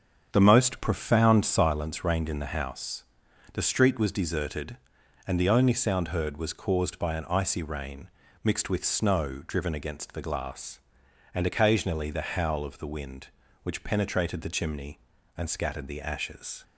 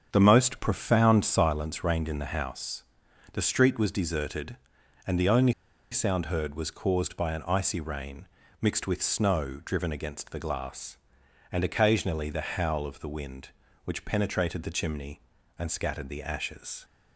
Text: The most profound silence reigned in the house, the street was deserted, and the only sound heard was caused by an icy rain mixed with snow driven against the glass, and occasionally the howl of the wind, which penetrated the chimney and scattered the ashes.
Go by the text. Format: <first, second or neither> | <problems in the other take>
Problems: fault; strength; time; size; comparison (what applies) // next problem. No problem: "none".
first | starts louder than the rest; strong; until 1.1 s; 7 dB; strong in the first // pauses between "only" and "sound"; at 5.5 s; 0.38 s long // pauses between "rain" and "mixed"; slight; at 8.2 s; 0.34 s long; slight in the first